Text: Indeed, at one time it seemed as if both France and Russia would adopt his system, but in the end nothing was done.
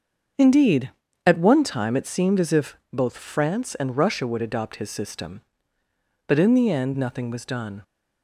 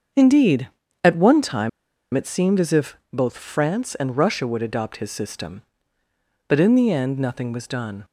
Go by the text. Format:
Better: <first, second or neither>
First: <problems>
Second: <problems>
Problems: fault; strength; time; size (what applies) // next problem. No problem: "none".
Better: first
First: starts louder than the rest; until 1.7 s; 7 dB // pauses between "if" and "both"; slight; at 2.7 s; 0.16 s long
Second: starts louder than the rest; until 1.4 s; 7 dB // pauses between "time" and "it"; at 1.6 s; 0.45 s long // pauses between "if" and "both"; slight; at 2.9 s; 0.16 s long